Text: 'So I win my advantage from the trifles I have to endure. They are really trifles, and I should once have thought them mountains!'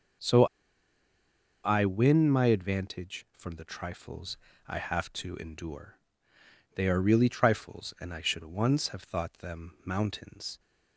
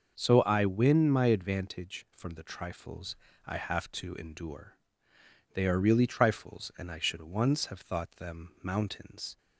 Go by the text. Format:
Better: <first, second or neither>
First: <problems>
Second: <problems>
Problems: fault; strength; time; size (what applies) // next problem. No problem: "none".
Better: second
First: starts louder than the rest; until 2.4 s; 6.5 dB // pauses between "So" and "I"; at 0.4 s; 1.2 s long // pauses between "trifles" and "I"; slight; at 4.3 s; 0.30 s long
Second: starts louder than the rest; until 1.2 s; 6 dB // pauses between "trifles" and "I"; slight; at 3.1 s; 0.30 s long